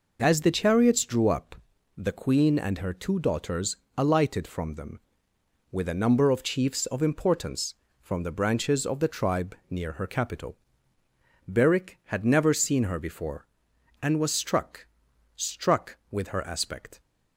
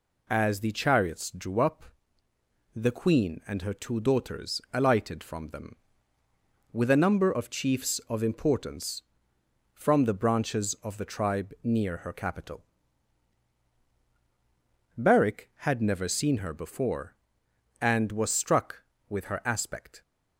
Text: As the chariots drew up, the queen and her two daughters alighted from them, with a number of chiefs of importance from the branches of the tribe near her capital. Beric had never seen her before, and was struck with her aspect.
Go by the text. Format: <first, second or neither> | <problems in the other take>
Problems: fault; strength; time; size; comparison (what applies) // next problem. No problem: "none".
second | pauses between "daughters" and "alighted"; slight; at 3.7 s; 0.20 s long // says "struck" twice; at 15.3 s